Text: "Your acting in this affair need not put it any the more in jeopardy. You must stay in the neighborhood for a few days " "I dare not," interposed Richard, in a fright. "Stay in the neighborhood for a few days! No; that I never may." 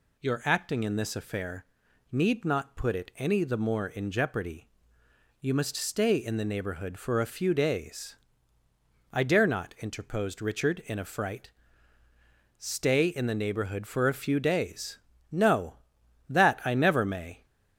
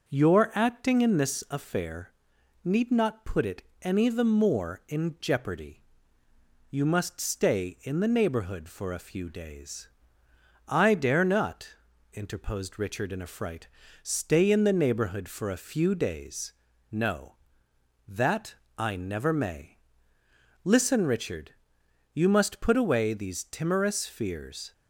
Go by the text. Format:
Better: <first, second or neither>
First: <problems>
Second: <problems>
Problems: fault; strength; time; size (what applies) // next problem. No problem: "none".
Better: first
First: pauses between "affair" and "need"; noticeable; at 1.6 s; 0.46 s long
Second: starts louder than the rest; until 1.1 s; 6 dB // pauses between "affair" and "need"; noticeable; at 2.1 s; 0.50 s long // pauses between "it" and "any"; slight; at 3.6 s; 0.20 s long // pauses between "that" and "I"; slight; at 18.5 s; 0.24 s long // goes on to say "Listen Richard You must put away these timorous fears"; strong; from 20.6 s on; 4.1 s long